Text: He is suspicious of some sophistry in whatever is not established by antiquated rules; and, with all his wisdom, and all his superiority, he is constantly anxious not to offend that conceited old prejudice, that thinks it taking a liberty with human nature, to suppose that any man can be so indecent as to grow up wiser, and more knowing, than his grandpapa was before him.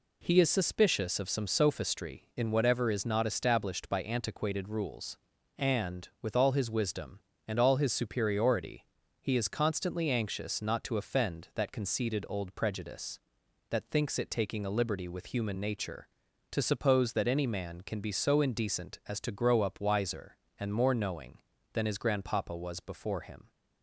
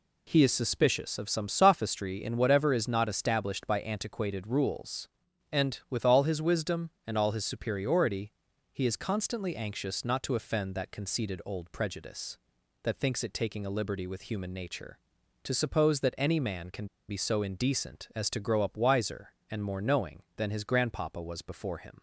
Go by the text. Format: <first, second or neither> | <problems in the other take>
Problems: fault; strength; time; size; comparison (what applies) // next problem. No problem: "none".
first | pauses between "can" and "be"; slight; at 16.8 s; 0.22 s long